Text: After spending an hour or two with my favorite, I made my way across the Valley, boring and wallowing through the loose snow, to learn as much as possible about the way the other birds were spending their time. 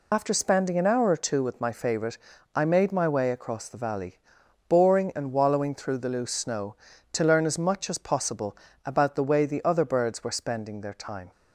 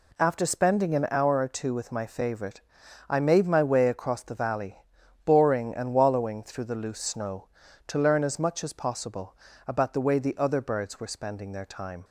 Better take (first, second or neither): second